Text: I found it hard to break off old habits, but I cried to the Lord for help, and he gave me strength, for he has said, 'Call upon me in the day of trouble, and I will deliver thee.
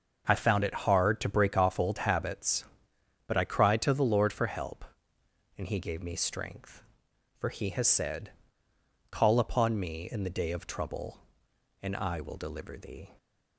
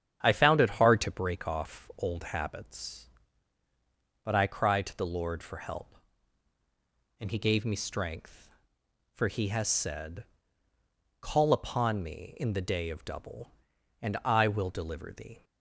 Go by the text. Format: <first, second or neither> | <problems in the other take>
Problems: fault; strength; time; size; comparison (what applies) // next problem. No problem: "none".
first | starts louder than the rest; strong; until 1.2 s; 9 dB; also in the first // says "double" for "trouble"; at 13.0 s